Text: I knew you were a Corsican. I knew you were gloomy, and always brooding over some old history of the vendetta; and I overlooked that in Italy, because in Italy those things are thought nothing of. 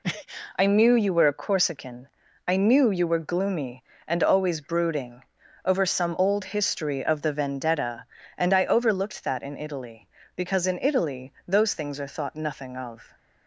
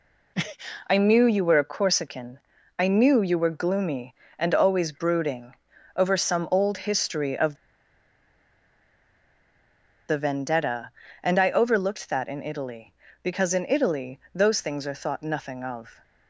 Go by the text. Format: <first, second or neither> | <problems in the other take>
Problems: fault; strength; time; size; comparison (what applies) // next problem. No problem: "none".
first | pauses between "brooding" and "over"; at 5.5 s; 0.42 s long; also in the first // pauses between "of" and "the"; strong; at 7.5 s; 2.5 s long